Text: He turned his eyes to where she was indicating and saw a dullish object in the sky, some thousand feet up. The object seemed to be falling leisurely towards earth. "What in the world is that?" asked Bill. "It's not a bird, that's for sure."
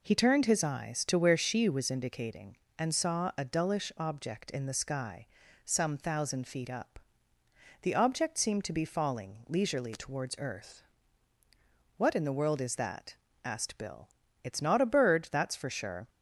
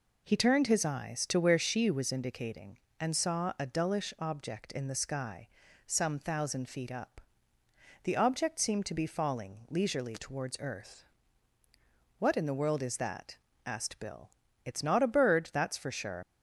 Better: first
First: none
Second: leaves "sure" unfinished; at 16.2 s; 70 ms

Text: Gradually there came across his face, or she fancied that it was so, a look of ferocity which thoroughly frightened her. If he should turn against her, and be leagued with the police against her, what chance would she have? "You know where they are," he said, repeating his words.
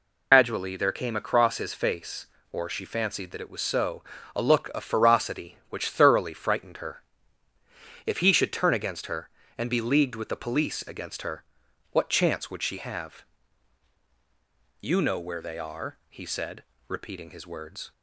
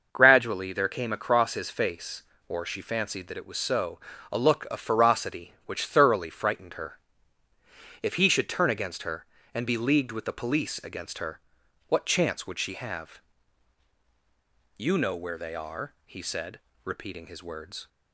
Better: second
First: loses the start of "Gradually"; at 0.3 s; 160 ms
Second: none

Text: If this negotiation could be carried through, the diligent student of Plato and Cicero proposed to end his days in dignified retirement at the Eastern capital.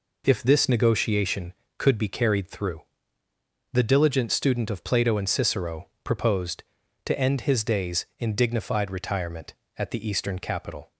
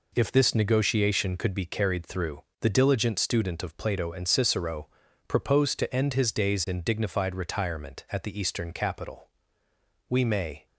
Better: first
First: pauses between "Cicero" and "proposed"; slight; at 5.8 s; 0.16 s long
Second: pauses between "Cicero" and "proposed"; at 4.8 s; 0.40 s long // goes on to say "We may"; from 10.0 s on; 0.58 s long

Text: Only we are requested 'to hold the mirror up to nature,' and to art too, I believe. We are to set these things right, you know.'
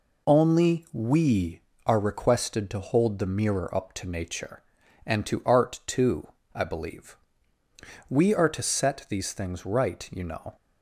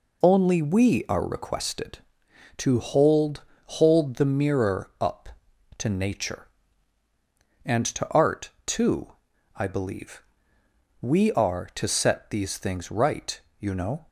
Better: first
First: none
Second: says "hold" twice; at 3.6 s // pauses between "art" and "too"; slight; at 8.4 s; 0.16 s long

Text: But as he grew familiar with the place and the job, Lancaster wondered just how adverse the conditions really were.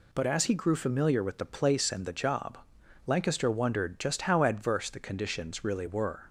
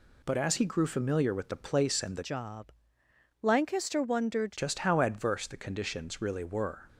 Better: first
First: none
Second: changes voice from "job" to "wondered"; from 2.2 to 4.5 s; 2.3 s long

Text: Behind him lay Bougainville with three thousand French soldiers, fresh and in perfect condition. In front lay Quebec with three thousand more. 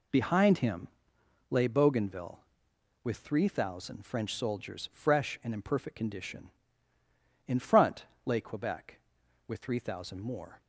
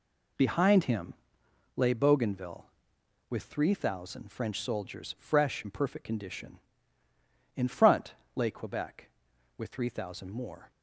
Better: first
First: pauses between "him" and "lay"; noticeable; at 0.8 s; 0.62 s long // pauses between "front" and "lay"; slight; at 8.0 s; 0.18 s long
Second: pauses between "him" and "lay"; noticeable; at 1.1 s; 0.62 s long // skips "and"; at 5.6 s // pauses between "front" and "lay"; slight; at 8.1 s; 0.20 s long

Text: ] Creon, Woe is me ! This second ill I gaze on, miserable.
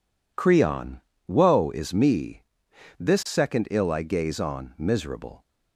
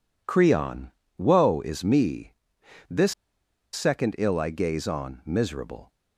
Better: first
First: none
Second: pauses between "This" and "second"; noticeable; at 3.1 s; 0.60 s long

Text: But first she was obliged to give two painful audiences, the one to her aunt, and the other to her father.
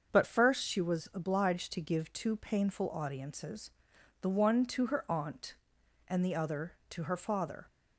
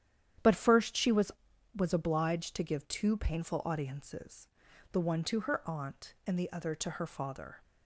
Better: first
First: starts louder than the rest; until 1.1 s; 6.5 dB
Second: starts louder than the rest; strong; until 1.8 s; 10 dB // says "was" twice; at 1.7 s

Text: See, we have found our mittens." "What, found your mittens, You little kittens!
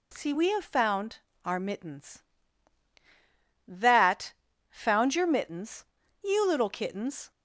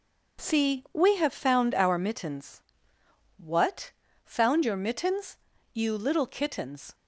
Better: second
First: pauses between "found" and "our"; slight; at 1.1 s; 0.26 s long // says "That" for "What"; at 3.6 s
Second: none

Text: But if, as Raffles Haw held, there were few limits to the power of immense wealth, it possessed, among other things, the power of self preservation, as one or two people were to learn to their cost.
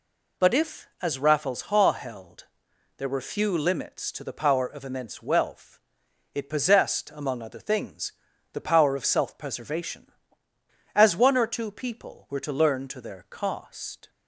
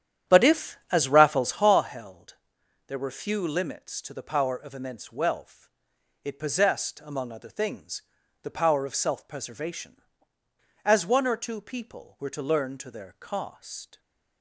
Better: first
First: none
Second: starts louder than the rest; strong; until 1.9 s; 10 dB

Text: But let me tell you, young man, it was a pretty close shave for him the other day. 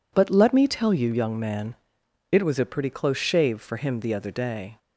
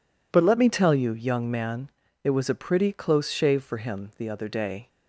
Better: neither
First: none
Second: none

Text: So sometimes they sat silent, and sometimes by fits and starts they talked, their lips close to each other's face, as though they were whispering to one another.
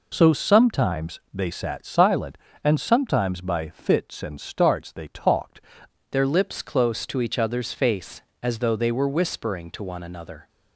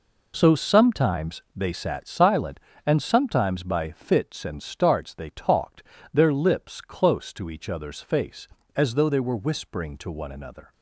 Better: second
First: changes voice at "their"; from 6.1 s on; 4.3 s long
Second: none

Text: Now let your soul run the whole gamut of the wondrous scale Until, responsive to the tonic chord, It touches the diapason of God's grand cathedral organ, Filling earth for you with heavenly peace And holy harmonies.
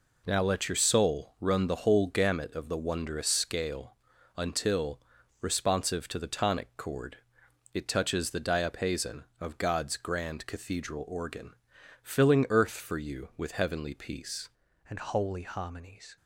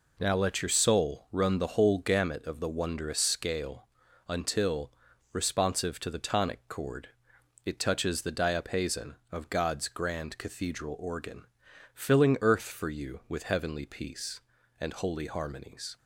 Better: second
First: pauses between "scale" and "Until"; at 3.9 s; 0.42 s long // changes voice at "And"; from 14.8 s on; 1.3 s long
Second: pauses between "scale" and "Until"; at 3.8 s; 0.42 s long

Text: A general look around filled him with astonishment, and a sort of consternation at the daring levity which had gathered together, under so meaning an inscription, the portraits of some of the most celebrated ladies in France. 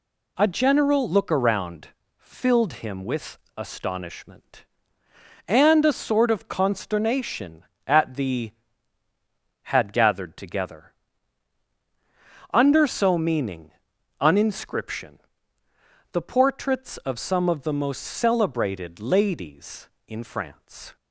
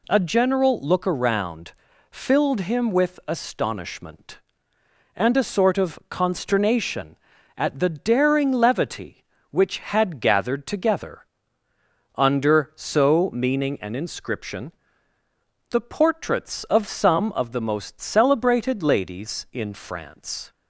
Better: second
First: pauses between "around" and "filled"; slight; at 1.8 s; 0.30 s long // pauses between "with" and "astonishment"; slight; at 3.3 s; 0.18 s long // skips "daring levity which"; at 9.0 s // pauses between "meaning" and "an"; noticeable; at 13.7 s; 0.48 s long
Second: pauses between "around" and "filled"; at 1.7 s; 0.38 s long

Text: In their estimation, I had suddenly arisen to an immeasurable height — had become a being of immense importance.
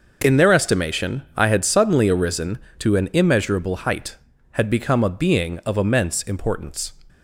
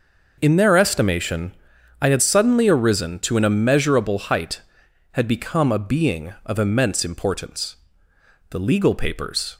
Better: first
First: none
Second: goes on to say "The legal papers"; noticeable; from 8.5 s on; 1.0 s long

